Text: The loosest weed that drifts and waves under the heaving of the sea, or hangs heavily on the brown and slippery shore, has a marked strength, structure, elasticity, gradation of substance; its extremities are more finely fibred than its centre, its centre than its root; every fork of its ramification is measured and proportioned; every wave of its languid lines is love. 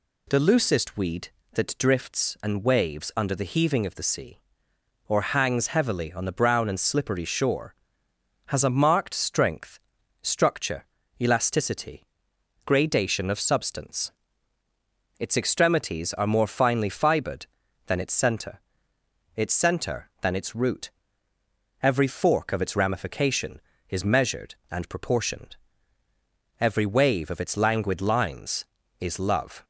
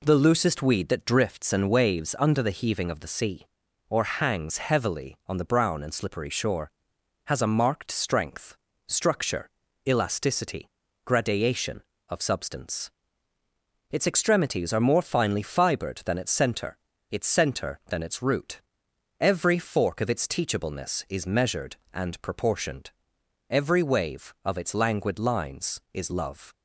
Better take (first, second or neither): first